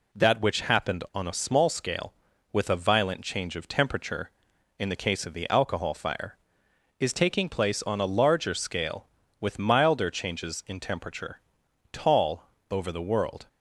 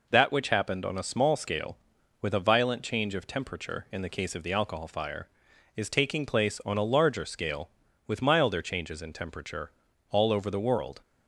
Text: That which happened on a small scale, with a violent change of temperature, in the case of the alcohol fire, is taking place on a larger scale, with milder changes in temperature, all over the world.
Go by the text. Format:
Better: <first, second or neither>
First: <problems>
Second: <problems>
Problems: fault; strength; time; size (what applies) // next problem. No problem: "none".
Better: second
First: says "tall" for "all"; at 11.9 s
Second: none